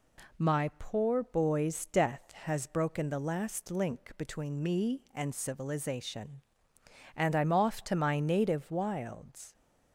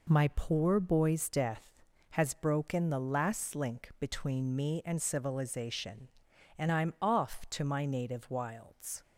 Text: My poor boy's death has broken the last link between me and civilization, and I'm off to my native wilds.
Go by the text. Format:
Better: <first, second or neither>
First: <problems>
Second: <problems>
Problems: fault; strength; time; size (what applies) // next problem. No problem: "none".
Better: neither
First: none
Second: none